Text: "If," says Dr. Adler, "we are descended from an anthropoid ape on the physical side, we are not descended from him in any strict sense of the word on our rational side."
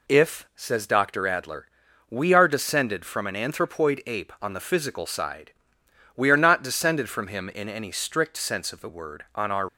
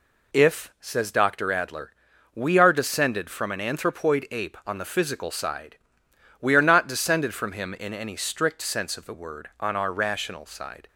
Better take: second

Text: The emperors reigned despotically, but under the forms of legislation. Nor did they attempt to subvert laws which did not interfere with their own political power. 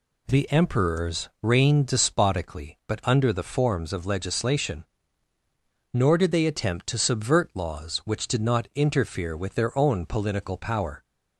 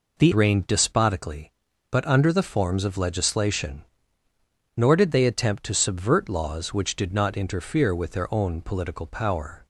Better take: first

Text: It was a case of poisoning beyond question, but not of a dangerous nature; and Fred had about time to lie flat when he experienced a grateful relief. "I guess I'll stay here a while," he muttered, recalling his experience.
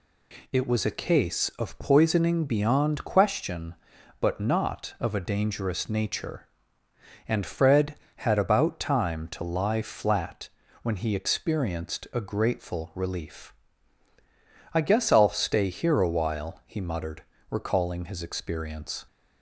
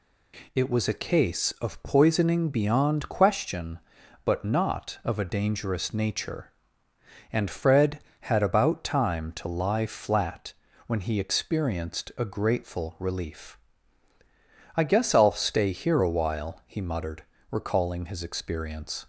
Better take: neither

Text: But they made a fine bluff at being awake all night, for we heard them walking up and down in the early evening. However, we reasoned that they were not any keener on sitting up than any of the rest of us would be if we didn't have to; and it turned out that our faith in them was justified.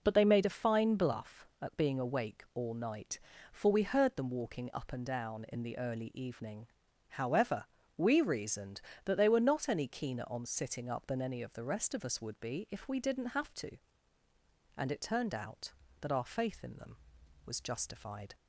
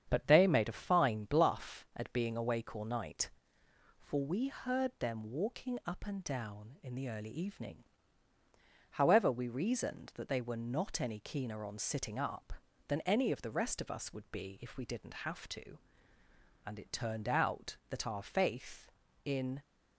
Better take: first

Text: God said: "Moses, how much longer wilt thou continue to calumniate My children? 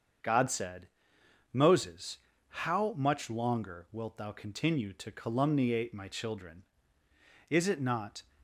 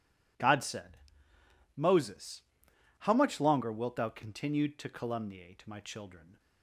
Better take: second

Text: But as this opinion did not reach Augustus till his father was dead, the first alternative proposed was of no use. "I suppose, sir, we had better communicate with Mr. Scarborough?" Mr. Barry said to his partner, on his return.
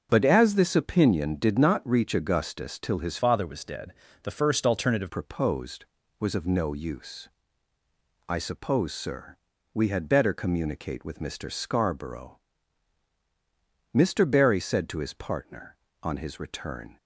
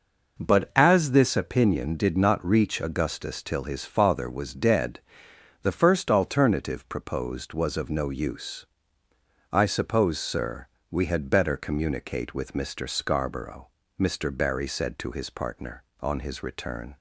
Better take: second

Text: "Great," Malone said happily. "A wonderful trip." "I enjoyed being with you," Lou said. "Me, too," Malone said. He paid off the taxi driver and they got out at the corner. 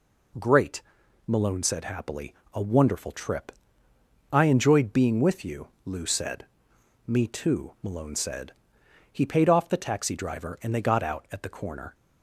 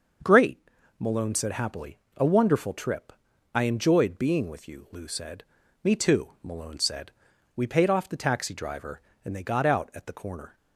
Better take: first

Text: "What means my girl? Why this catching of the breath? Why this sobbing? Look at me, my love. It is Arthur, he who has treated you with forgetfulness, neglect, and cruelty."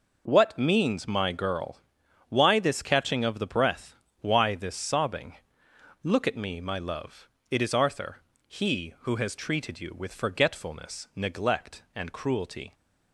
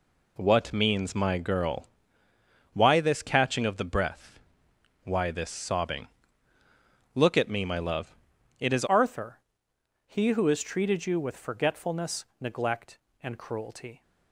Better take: first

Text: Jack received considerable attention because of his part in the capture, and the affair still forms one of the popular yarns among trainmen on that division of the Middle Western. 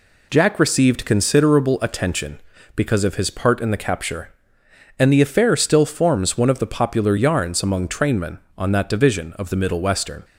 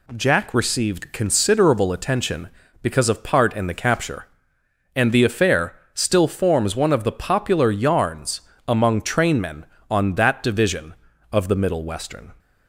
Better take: first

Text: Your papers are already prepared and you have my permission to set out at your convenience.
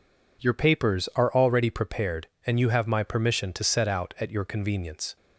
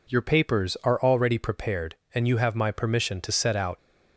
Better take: first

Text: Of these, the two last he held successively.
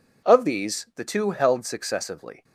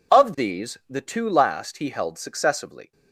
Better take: second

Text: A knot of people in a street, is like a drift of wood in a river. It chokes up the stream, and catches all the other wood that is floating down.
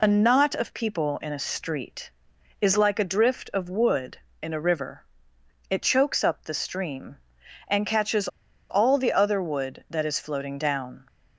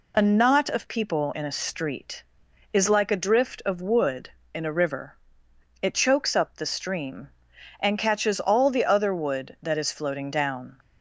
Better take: second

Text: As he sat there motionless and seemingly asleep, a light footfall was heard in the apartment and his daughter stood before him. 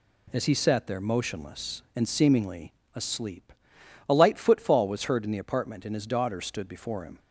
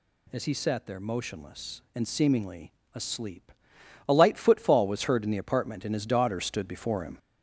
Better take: first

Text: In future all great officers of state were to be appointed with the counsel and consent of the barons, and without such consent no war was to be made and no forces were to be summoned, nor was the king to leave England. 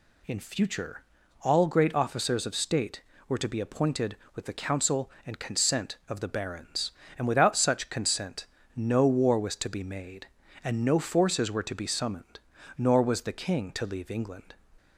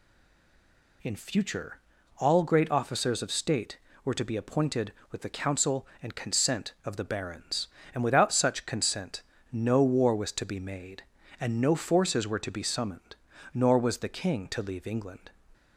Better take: first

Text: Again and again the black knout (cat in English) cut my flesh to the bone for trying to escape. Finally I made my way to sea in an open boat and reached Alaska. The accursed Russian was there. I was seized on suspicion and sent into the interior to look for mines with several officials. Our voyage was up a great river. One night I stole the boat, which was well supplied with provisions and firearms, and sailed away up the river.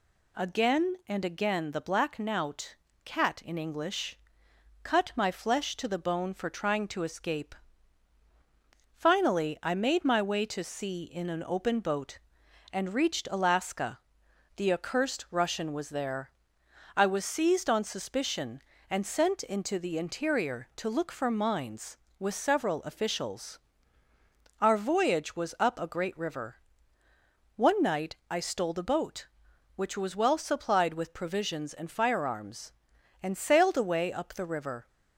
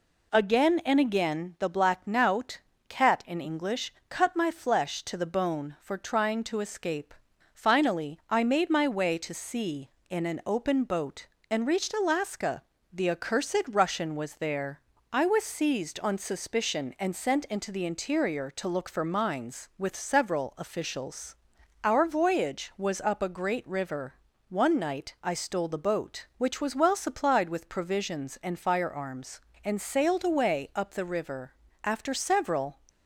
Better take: first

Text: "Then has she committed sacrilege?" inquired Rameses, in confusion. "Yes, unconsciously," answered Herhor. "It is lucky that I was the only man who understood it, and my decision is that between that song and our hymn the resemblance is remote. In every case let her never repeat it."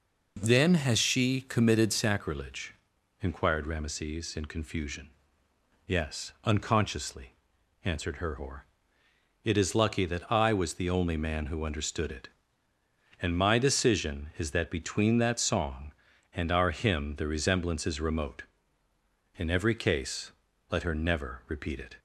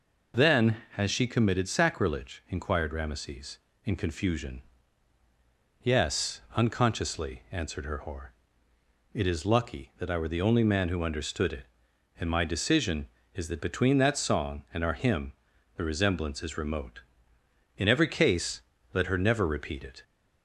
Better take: first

